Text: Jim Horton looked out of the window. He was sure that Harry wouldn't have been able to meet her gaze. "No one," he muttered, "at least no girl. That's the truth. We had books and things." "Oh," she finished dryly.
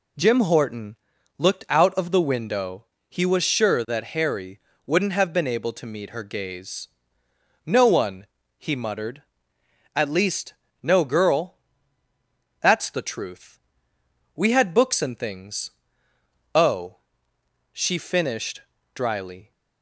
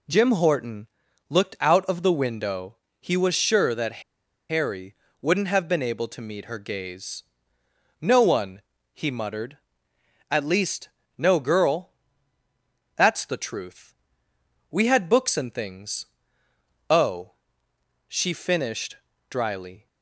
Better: first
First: pauses between "Horton" and "looked"; at 0.9 s; 0.44 s long // pauses between "Harry" and "wouldn't"; slight; at 4.5 s; 0.26 s long // pauses between "least" and "no"; slight; at 10.5 s; 0.28 s long // pauses between "finished" and "dryly"; slight; at 18.6 s; 0.34 s long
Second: pauses between "Horton" and "looked"; at 0.8 s; 0.44 s long // pauses between "that" and "Harry"; noticeable; at 4.0 s; 0.47 s long // pauses between "Harry" and "wouldn't"; slight; at 4.9 s; 0.26 s long // pauses between "least" and "no"; slight; at 10.8 s; 0.28 s long // pauses between "finished" and "dryly"; slight; at 18.9 s; 0.34 s long

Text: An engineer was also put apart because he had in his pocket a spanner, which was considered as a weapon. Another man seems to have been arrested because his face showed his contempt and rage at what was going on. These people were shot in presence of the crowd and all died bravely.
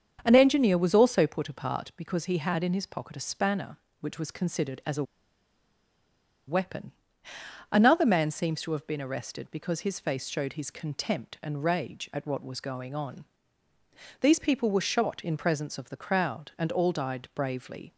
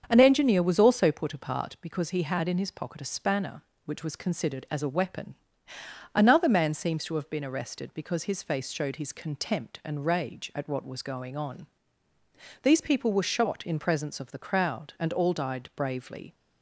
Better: second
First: starts louder than the rest; strong; until 1.2 s; 7.5 dB // pauses between "a" and "weapon"; strong; at 5.0 s; 1.4 s long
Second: starts louder than the rest; strong; until 1.0 s; 7.5 dB

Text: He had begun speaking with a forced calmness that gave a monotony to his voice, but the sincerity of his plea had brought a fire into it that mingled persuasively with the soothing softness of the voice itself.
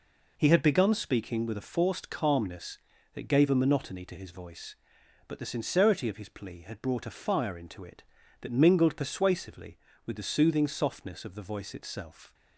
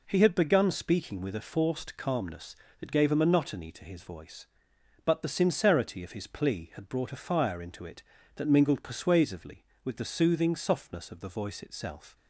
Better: neither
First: none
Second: none

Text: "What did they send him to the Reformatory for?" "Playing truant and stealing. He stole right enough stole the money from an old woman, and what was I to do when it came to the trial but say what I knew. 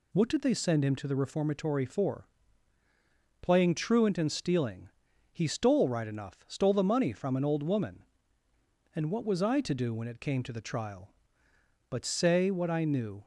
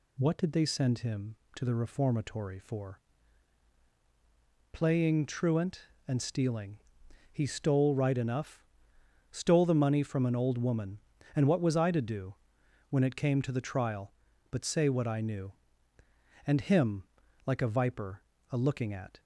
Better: first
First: none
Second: pauses between "enough" and "stole"; noticeable; at 8.6 s; 0.66 s long // pauses between "do" and "when"; noticeable; at 12.3 s; 0.56 s long // goes on to say "And him like a viper a looking at"; strong; from 16.4 s on; 2.7 s long

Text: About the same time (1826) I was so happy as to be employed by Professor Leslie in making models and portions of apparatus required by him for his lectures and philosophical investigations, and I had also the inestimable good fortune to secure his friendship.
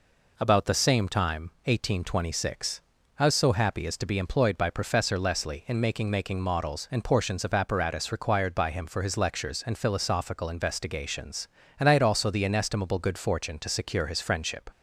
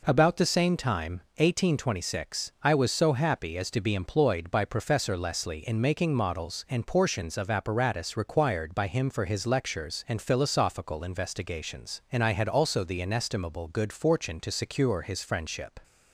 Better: second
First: says "making" twice; at 6.0 s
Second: none

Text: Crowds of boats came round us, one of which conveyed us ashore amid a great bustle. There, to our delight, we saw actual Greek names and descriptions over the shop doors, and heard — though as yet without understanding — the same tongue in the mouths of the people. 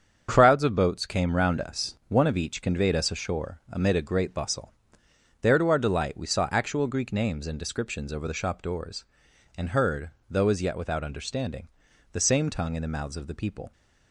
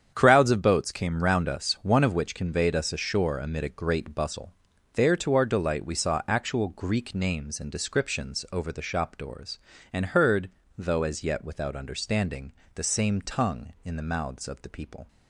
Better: second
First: starts louder than the rest; strong; until 1.3 s; 7.5 dB // says "each" for "which"; at 2.3 s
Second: starts louder than the rest; strong; until 1.1 s; 8.5 dB

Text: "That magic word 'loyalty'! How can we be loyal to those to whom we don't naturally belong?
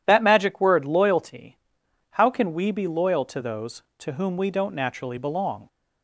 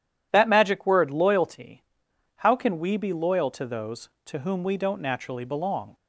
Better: neither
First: none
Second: none

